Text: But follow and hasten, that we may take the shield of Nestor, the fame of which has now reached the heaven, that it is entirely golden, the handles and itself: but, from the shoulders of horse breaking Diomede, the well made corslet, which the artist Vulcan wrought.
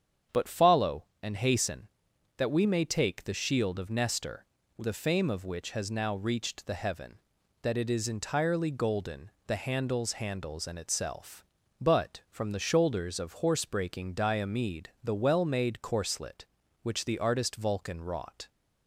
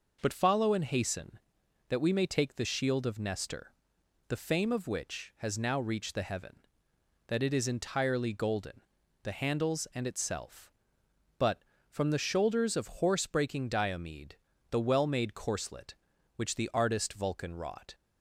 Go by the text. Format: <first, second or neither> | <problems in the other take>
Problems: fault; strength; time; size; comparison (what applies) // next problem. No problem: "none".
second | starts louder than the rest; strong; until 1.5 s; 8 dB // says "handles" twice; at 10.1 s